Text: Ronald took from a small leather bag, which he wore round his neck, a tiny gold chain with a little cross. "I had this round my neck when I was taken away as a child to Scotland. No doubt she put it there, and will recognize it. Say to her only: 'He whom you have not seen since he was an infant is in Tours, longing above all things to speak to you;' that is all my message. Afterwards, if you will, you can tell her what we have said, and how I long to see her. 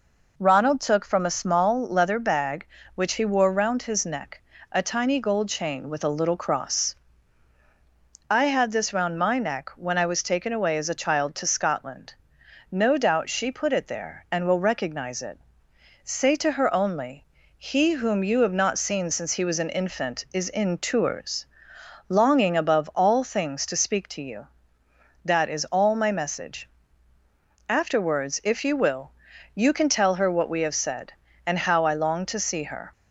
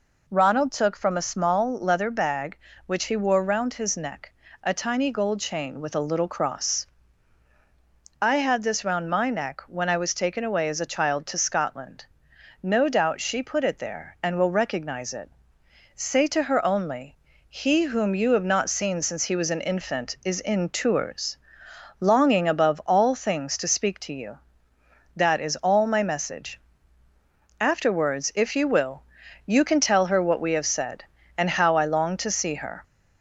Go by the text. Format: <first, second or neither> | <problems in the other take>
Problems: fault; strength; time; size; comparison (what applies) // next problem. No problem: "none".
first | gets louder; slight; throughout; 3 dB